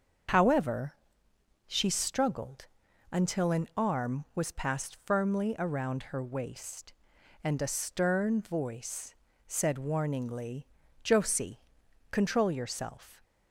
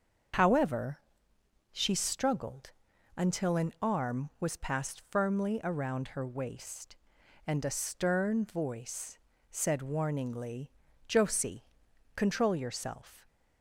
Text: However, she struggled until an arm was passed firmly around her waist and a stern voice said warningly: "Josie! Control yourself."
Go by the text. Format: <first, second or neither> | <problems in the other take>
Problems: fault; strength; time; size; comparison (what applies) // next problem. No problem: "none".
neither | starts louder than the rest; the same in both // pauses between "struggled" and "until"; the same in both // pauses between "voice" and "said"; slight; the same in both